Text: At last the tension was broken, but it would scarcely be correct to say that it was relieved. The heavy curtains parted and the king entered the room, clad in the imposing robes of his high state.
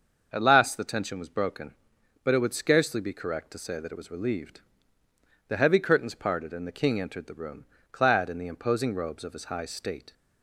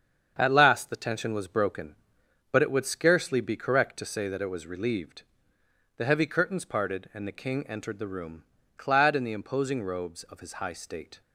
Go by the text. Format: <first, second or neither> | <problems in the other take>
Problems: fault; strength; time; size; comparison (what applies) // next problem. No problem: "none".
neither | starts louder than the rest; the same in both